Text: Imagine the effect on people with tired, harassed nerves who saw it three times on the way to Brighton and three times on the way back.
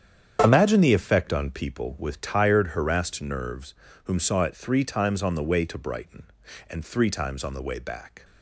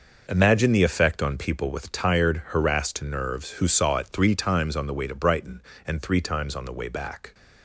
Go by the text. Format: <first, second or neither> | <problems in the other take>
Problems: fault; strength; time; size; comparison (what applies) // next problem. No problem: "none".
second | starts louder than the rest; strong; until 1.4 s; 8 dB // says "whom" for "who"; at 4.0 s